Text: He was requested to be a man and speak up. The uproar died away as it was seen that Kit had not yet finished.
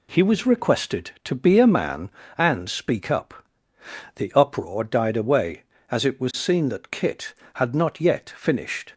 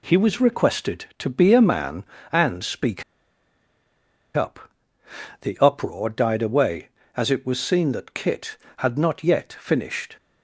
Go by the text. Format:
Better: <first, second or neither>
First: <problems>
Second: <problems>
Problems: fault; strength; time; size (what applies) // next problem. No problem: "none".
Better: first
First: none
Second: pauses between "speak" and "up"; strong; at 3.0 s; 1.3 s long